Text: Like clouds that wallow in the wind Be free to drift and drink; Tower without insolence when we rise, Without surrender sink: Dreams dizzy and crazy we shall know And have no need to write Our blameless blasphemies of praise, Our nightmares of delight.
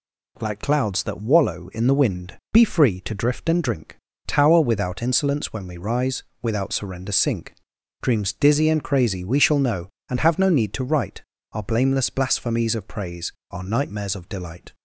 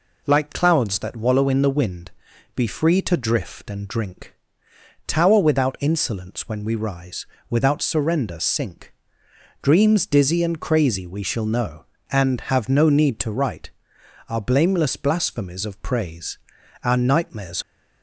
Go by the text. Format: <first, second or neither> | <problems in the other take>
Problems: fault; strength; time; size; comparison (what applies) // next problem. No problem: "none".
first | pauses between "wind" and "Be"; at 2.1 s; 0.44 s long; slight in the first // pauses between "write" and "Our"; noticeable; at 13.7 s; 0.58 s long; slight in the first // stops before "of delight"; at 17.6 s